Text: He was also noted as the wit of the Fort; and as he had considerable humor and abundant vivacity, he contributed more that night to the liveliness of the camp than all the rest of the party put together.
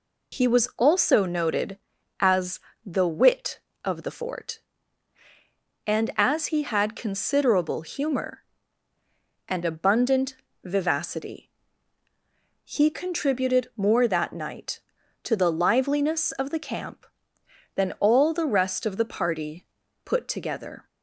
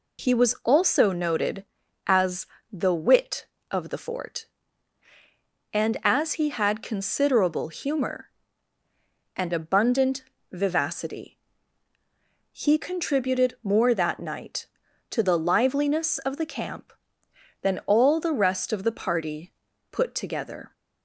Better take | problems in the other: neither | pauses between "as" and "the"; slight; the same in both // pauses between "abundant" and "vivacity"; slight; the same in both // pauses between "party" and "put"; the same in both

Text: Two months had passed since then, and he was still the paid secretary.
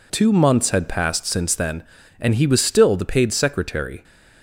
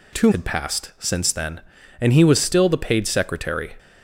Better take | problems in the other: first | skips "months"; at 0.3 s

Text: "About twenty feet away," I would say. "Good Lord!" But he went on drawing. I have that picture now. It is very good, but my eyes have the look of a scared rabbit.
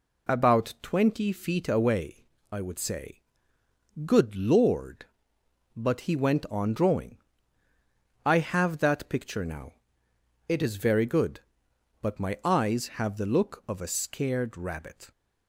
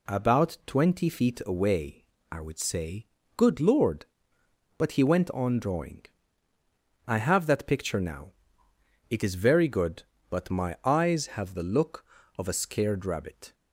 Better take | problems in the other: neither | none

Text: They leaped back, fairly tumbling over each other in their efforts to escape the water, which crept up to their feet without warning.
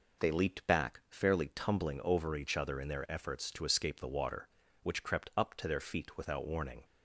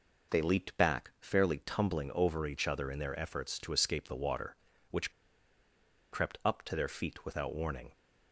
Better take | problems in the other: first | pauses between "which" and "crept"; at 5.1 s; 1.0 s long

